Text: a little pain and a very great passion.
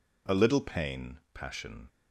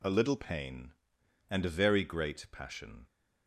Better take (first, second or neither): second